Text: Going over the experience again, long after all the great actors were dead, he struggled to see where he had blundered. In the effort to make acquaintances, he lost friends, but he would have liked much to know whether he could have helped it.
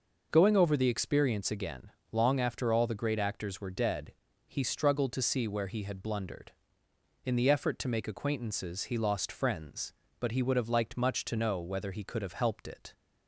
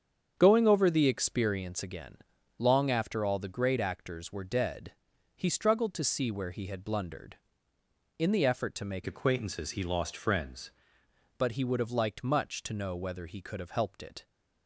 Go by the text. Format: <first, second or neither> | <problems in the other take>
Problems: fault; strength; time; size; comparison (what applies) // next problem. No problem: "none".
first | starts louder than the rest; strong; until 1.4 s; 7.5 dB // changes voice from "acquaintances" to "friends"; from 9.0 to 10.7 s; 1.7 s long